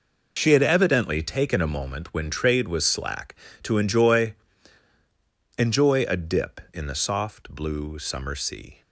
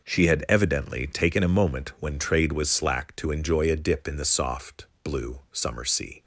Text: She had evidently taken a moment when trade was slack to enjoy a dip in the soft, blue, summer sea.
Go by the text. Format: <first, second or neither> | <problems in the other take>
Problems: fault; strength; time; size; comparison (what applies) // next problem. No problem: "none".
second | says "enjoy" twice; at 5.5 s